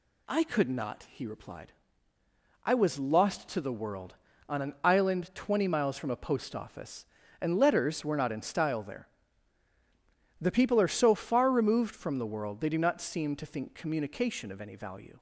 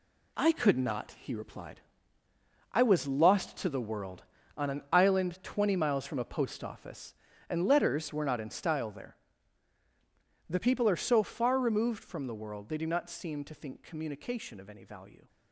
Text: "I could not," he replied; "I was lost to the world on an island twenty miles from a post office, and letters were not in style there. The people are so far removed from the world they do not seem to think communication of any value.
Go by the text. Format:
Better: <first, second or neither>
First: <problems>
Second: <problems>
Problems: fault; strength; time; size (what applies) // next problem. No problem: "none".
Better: first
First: none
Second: gets quieter; strong; throughout; 8.5 dB